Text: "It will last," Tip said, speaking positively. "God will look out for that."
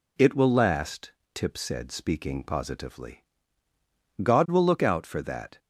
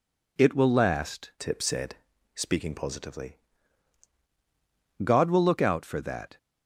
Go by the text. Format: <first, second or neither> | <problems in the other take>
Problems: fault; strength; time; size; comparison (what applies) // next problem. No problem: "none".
first | changes voice from "Tip" to "positively"; from 1.3 to 3.3 s; 2.0 s long